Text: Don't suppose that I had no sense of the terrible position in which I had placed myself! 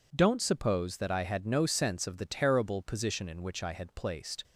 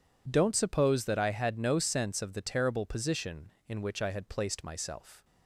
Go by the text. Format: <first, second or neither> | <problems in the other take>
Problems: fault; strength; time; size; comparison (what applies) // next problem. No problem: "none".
second | stops before "myself"; at 4.4 s